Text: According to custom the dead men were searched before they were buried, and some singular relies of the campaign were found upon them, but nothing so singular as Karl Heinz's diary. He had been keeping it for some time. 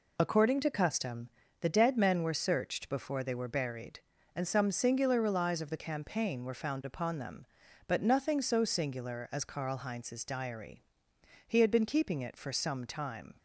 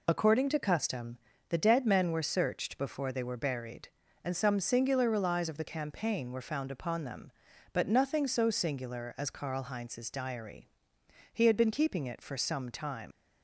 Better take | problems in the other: first | pauses between "custom" and "the"; slight; at 1.1 s; 0.32 s long; slight in the first // leaves "time" unfinished; at 13.1 s; 120 ms

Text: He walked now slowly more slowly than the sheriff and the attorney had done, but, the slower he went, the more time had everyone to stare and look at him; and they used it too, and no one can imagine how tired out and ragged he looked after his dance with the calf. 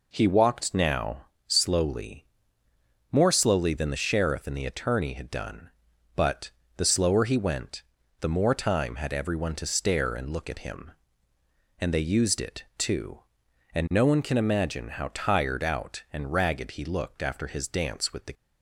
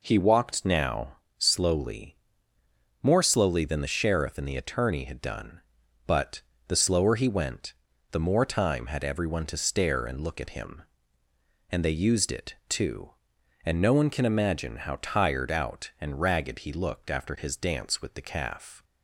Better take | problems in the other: second | pauses between "now" and "slowly"; slight; at 1.2 s; 0.24 s long; slight in the second // pauses between "slowly" and "more"; noticeable; at 2.2 s; 0.86 s long; noticeable in the second // stops before "calf"; at 18.3 s

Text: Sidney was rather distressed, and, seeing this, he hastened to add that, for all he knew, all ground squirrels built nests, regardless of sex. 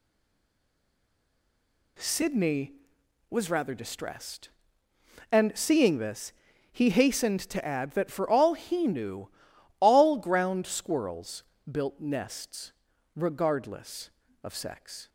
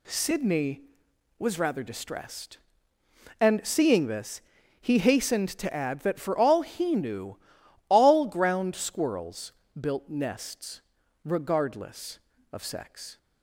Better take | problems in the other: second | stays silent before the first word; noticeable; until 1.9 s; 1.9 s long // pauses between "squirrels" and "built"; slight; at 11.4 s; 0.28 s long; slight in the second

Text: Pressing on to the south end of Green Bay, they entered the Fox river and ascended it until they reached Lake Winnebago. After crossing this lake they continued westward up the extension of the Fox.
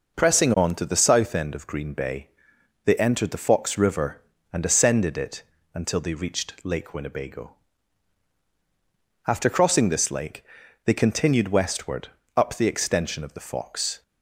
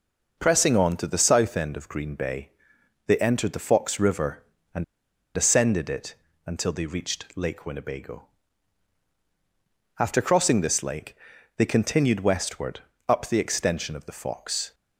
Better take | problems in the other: first | pauses between "and" and "ascended"; noticeable; at 4.8 s; 0.51 s long // pauses between "it" and "until"; slight; at 6.1 s; 0.32 s long; slight in the first // pauses between "lake" and "they"; at 11.1 s; 0.40 s long; also in the first // pauses between "westward" and "up"; slight; at 12.7 s; 0.28 s long; slight in the first

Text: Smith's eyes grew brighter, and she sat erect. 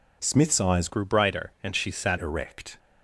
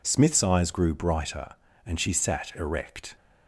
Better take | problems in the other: second | changes voice from "grew" to "sat"; from 0.8 to 2.1 s; 1.3 s long

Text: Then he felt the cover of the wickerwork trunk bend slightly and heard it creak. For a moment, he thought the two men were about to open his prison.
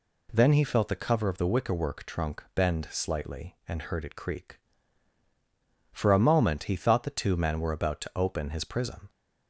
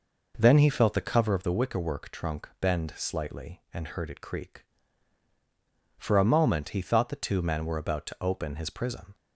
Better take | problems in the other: first | starts louder than the rest; noticeable; until 1.5 s; 5 dB

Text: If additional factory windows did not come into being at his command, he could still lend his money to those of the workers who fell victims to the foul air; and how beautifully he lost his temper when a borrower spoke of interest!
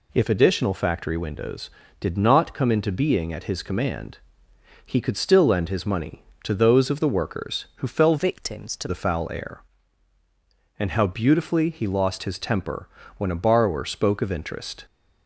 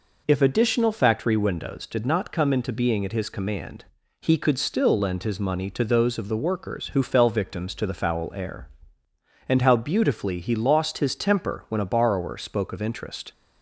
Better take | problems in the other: second | changes voice from "victims" to "to"; from 8.1 to 8.8 s; 0.7 s long // pauses between "temper" and "when"; slight; at 12.8 s; 0.30 s long

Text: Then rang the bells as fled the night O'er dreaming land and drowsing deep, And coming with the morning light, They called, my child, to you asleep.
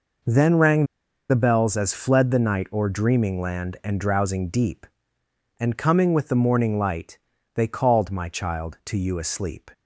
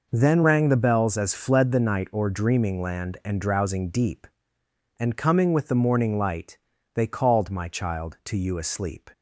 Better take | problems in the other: second | pauses between "rang" and "the"; at 0.8 s; 0.45 s long

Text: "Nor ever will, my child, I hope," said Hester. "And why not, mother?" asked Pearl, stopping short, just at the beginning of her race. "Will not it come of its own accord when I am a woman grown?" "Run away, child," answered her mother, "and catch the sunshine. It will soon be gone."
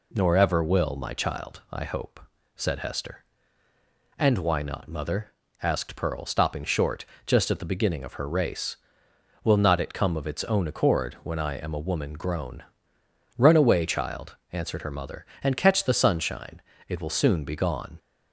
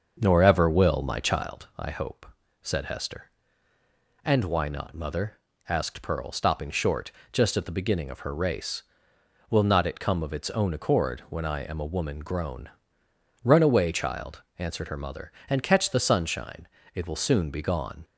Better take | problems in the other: first | starts louder than the rest; until 1.5 s; 6.5 dB

